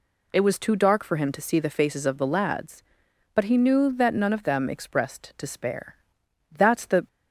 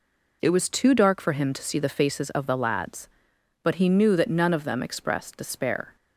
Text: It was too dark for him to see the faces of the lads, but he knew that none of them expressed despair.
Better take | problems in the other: second | goes on to say "That's the"; from 6.5 s on; 0.56 s long

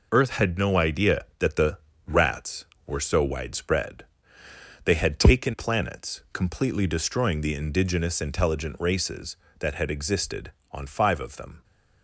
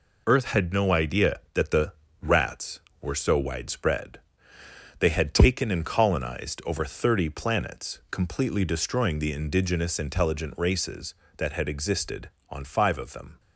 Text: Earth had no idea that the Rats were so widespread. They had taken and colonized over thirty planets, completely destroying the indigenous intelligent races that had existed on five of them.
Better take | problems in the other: second | pauses between "the" and "Rats"; slight; at 1.7 s; 0.32 s long; slight in the second // skips "and colonized over thirty"; at 5.5 s

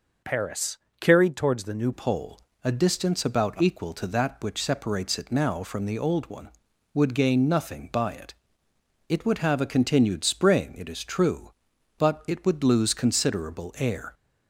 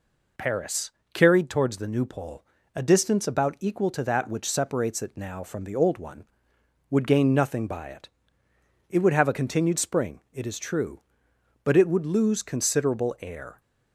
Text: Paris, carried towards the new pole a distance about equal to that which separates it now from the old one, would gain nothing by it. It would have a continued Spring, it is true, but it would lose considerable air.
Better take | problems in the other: second | changes voice at "pole"; from 1.9 s on; 12.2 s long // pauses between "pole" and "a"; slight; at 2.3 s; 0.24 s long; slight in the second

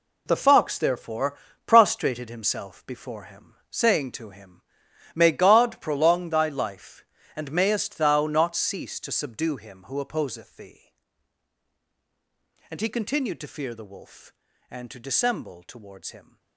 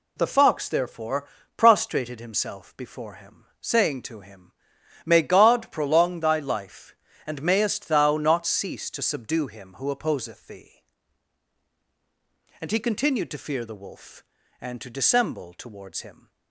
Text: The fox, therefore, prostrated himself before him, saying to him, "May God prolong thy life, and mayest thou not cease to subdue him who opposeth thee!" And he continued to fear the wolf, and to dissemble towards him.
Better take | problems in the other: second | gets quieter; strong; throughout; 10.5 dB

